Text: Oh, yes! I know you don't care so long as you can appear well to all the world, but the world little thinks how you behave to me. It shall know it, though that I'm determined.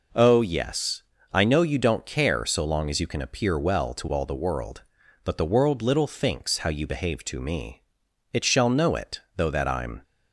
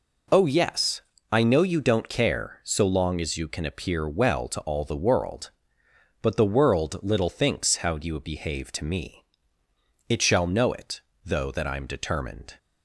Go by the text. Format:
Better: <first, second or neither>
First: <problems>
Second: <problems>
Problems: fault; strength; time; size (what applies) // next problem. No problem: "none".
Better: second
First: stops before "determined"; at 10.0 s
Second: none